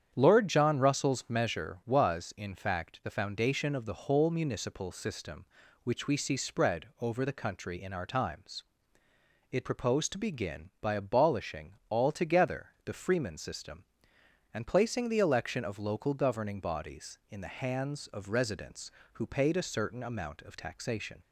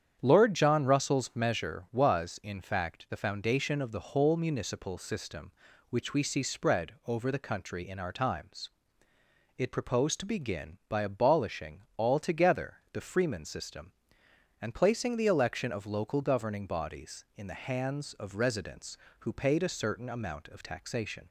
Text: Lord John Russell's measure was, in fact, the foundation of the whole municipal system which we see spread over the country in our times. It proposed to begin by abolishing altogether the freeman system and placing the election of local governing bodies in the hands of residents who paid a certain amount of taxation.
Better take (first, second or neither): neither